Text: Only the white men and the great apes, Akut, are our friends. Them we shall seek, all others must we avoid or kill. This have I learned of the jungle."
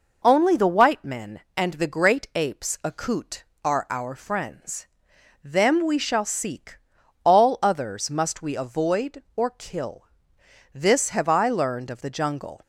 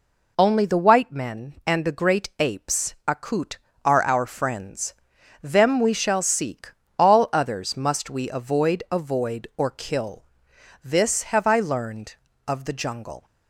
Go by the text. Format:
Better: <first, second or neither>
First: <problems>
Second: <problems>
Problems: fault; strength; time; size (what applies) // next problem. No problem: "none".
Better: first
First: none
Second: says "avoid" twice; at 8.9 s